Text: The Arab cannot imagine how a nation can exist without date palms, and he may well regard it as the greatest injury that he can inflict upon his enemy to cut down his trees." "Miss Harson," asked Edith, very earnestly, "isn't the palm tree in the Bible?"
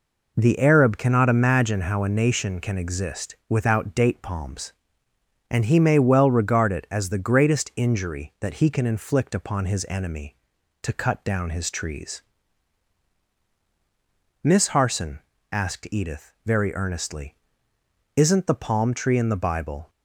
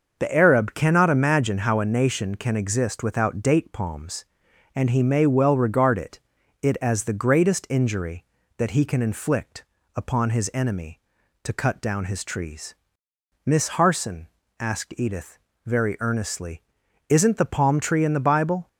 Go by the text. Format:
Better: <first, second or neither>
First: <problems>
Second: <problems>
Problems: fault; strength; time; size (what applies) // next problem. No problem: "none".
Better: first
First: none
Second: starts louder than the rest; noticeable; until 1.2 s; 6 dB // says "it" twice; at 6.5 s // pauses between "inflict" and "upon"; slight; at 9.6 s; 0.32 s long